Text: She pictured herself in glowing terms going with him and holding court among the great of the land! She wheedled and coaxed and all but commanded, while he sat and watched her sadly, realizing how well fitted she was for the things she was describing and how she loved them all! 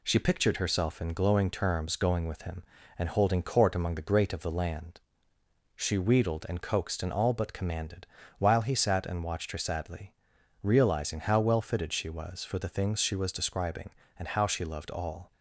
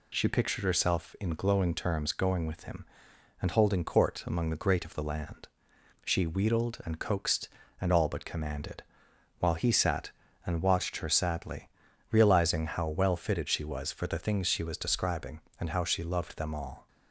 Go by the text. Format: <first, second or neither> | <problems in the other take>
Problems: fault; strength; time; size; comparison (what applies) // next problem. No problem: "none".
second | skips "them"; at 14.8 s